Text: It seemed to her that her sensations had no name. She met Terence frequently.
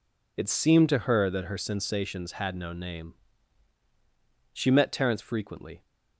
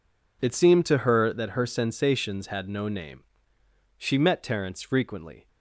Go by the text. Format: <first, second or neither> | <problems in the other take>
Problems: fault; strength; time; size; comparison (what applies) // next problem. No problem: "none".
neither | none